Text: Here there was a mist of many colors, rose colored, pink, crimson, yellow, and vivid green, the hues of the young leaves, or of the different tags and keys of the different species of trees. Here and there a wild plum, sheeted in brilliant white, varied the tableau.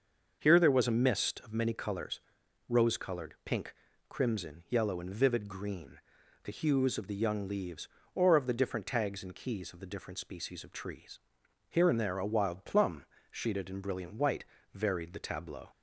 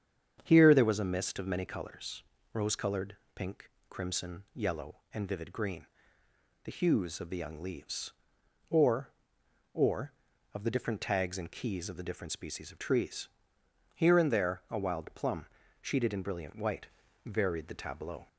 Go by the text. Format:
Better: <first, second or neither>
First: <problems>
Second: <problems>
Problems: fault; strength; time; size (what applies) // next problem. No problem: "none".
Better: first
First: starts louder than the rest; until 1.4 s; 6.5 dB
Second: starts louder than the rest; strong; until 1.4 s; 8 dB // says "or" twice; at 9.7 s